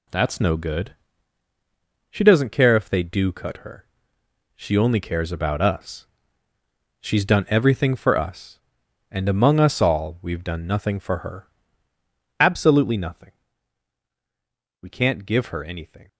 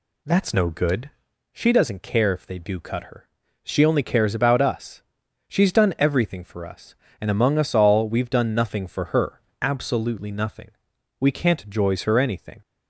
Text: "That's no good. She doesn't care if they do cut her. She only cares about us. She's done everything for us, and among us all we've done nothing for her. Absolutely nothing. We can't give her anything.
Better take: first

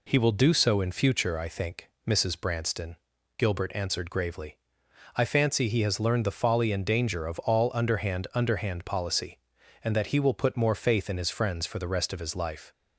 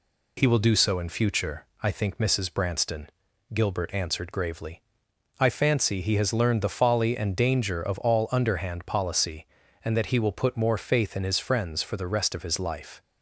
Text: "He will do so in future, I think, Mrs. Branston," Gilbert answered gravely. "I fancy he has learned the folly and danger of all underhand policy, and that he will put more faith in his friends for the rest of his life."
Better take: second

